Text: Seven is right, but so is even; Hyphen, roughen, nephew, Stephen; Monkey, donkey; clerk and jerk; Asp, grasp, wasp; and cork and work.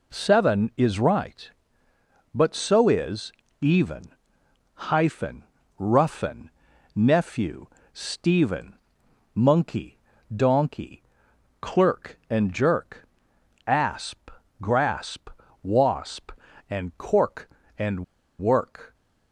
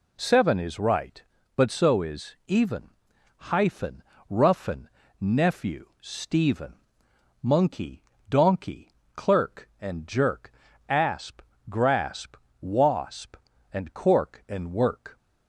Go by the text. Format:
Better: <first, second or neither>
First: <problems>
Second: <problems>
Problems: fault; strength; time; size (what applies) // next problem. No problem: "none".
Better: second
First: pauses between "is" and "even"; slight; at 3.3 s; 0.30 s long // pauses between "and" and "work"; slight; at 18.0 s; 0.35 s long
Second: none